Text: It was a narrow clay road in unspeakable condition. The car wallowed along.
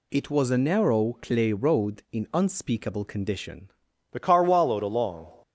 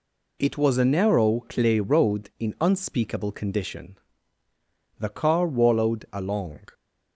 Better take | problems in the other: second | changes voice at "The"; from 4.1 s on; 1.2 s long

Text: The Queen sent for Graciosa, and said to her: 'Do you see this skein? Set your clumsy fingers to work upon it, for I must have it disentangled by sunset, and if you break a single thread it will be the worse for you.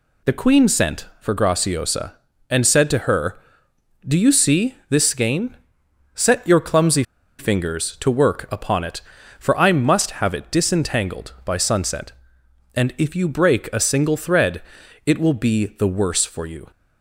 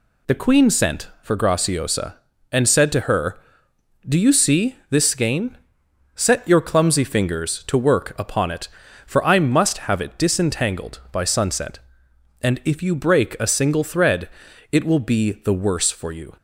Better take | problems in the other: second | pauses between "clumsy" and "fingers"; slight; at 7.0 s; 0.35 s long // pauses between "thread" and "it"; at 14.6 s; 0.42 s long; also in the second

